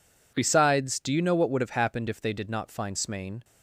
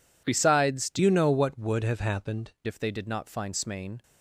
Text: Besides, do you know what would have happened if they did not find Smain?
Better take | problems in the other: first | changes voice from "you" to "happened"; from 0.9 to 2.5 s; 1.6 s long

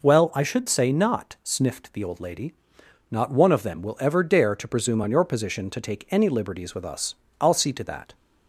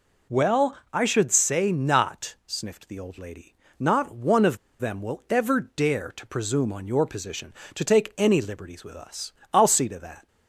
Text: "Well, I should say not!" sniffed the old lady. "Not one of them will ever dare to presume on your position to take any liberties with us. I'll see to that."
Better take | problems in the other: first | pauses between "of" and "them"; slight; at 4.5 s; 0.23 s long

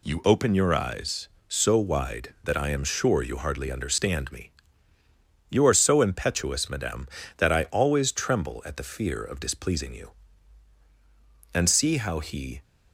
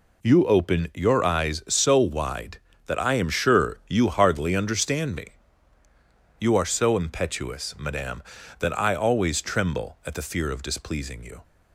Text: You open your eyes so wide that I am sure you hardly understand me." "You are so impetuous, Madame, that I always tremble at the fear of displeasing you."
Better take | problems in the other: second | goes on to say "And see how he"; noticeable; from 11.5 s on; 1.0 s long

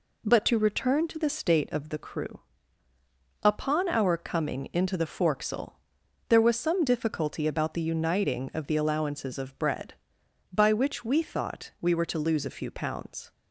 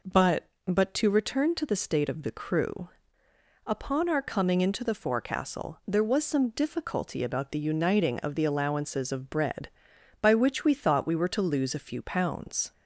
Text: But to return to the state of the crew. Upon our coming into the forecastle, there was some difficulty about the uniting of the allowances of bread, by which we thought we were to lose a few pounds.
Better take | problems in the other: first | says "But" twice; at 0.6 s

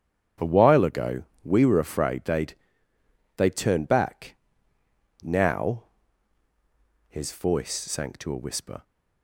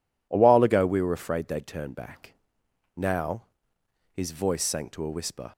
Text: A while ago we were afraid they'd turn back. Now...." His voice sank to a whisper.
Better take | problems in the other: second | starts louder than the rest; strong; until 1.6 s; 8 dB // pauses between "ago" and "we"; slight; at 1.2 s; 0.20 s long // says "they'd" twice; at 3.3 s

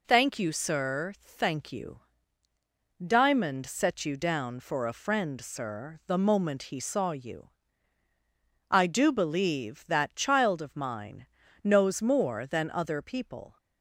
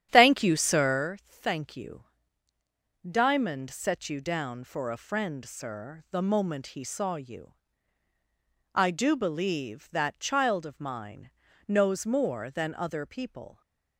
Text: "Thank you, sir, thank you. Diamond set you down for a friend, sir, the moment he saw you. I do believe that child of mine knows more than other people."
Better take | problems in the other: first | starts louder than the rest; strong; until 1.1 s; 10 dB // pauses between "mine" and "knows"; at 11.2 s; 0.38 s long; also in the first

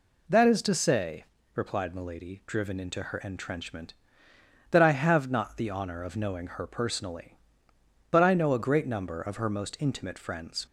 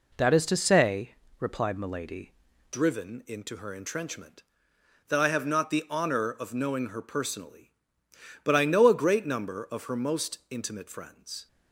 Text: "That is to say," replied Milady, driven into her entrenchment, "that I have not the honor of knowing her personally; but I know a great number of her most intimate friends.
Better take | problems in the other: first | changes voice at "driven"; from 2.7 s on; 8.7 s long

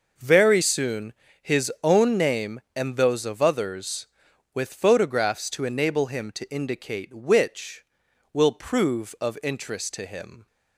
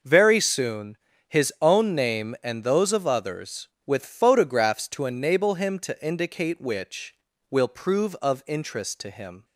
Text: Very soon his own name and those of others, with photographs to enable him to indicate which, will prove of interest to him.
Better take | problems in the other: neither | pauses between "soon" and "his"; slight; the same in both

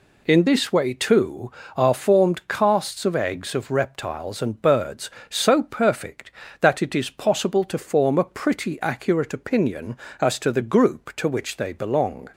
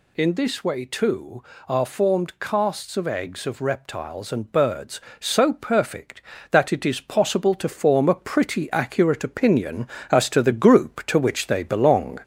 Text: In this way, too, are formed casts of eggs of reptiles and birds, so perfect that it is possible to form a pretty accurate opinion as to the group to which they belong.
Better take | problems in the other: first | gets louder; throughout; 4 dB

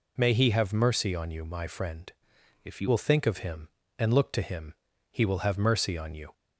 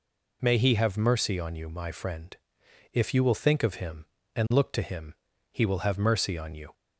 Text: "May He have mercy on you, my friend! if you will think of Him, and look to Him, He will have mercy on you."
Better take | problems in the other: second | changes voice from "if" to "you"; from 2.6 to 2.8 s; 0.2 s long

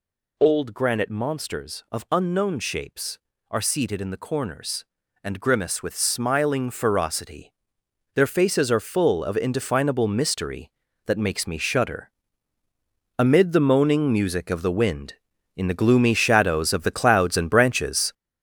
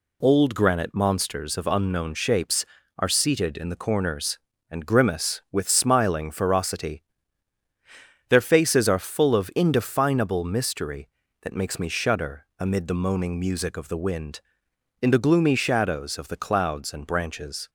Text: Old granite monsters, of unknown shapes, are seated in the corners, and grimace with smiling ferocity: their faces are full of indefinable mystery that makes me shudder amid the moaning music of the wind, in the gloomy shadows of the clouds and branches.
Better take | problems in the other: second | gets louder; throughout; 6.5 dB // pauses between "shudder" and "amid"; at 12.1 s; 1.0 s long

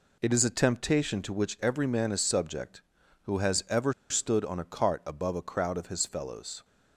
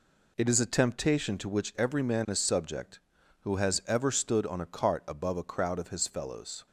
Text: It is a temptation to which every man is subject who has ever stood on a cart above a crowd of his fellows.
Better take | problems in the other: second | pauses between "ever" and "stood"; slight; at 3.9 s; 0.18 s long

